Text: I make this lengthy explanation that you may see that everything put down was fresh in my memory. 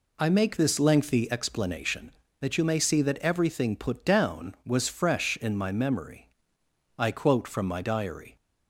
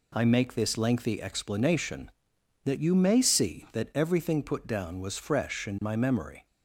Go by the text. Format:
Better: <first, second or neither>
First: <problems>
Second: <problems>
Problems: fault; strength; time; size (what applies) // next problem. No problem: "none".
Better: second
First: goes on to say "I quote from my diary"; from 6.9 s on; 1.3 s long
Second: none